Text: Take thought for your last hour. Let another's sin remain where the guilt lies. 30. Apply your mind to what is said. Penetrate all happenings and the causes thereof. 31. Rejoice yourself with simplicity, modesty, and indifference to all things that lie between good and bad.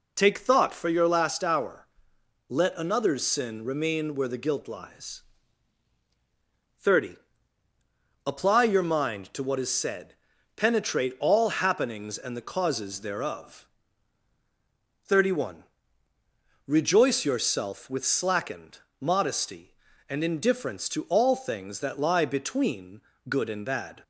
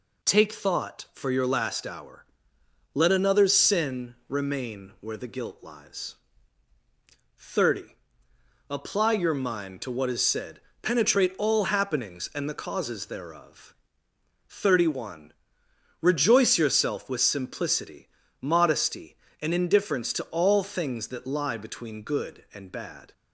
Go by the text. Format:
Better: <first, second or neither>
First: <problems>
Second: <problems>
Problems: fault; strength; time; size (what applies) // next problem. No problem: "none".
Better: second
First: says "slackened" for "simplicity"; at 18.0 s // pauses between "between" and "good"; slight; at 23.0 s; 0.26 s long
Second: none